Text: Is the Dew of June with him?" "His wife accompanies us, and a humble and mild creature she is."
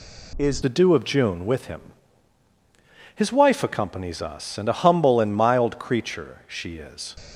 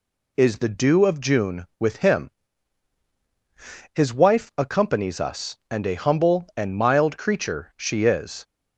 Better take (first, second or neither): second